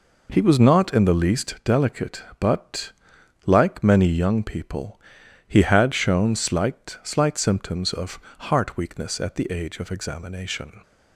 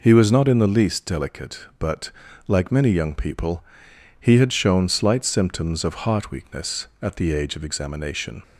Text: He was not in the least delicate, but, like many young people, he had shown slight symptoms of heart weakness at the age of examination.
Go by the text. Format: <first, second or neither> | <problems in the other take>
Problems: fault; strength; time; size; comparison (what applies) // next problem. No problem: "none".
second | says "slight" twice; at 7.0 s // pauses between "of" and "heart"; slight; at 8.1 s; 0.30 s long